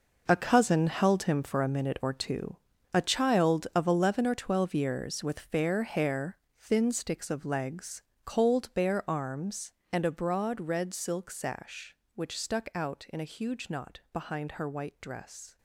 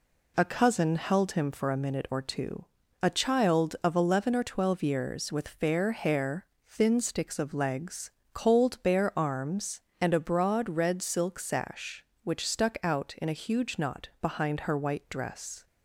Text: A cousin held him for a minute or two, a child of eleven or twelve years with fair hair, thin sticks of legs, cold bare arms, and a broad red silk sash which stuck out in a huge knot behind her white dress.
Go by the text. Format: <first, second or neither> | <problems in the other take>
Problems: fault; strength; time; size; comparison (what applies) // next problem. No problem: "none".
second | gets quieter; strong; throughout; 12.5 dB